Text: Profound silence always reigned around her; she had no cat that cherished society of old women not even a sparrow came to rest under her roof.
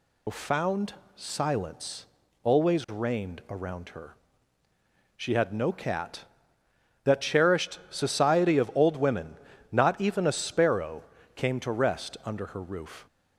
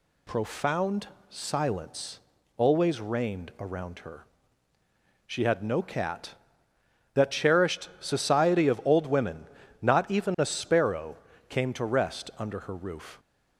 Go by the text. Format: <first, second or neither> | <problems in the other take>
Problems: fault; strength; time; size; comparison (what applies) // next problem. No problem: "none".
second | loses the start of "Profound"; at 0.2 s; 135 ms // pauses between "Profound" and "silence"; slight; at 0.9 s; 0.22 s long; slight in the second // pauses between "silence" and "always"; at 2.0 s; 0.38 s long; also in the second // pauses between "women" and "not"; slight; at 9.3 s; 0.34 s long; slight in the second // pauses between "sparrow" and "came"; slight; at 11.0 s; 0.32 s long; slight in the second